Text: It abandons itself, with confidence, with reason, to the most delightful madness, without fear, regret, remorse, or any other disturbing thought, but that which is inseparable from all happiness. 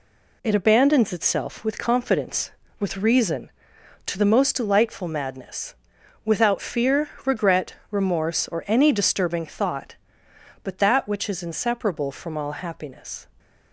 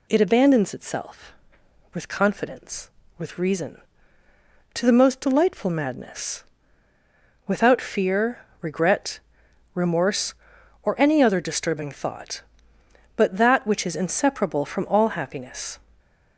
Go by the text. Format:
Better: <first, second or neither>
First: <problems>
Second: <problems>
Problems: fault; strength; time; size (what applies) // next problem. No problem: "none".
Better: second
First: skips "other"; at 8.9 s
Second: none